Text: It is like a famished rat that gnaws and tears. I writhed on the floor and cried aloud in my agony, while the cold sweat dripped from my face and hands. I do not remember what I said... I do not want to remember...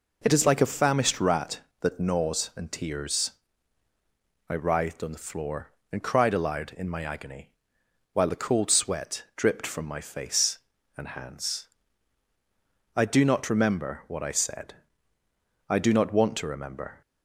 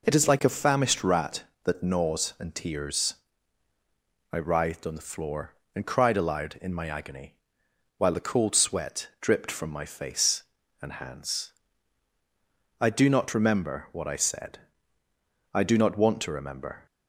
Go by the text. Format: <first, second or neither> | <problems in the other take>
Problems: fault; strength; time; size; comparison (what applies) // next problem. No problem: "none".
neither | none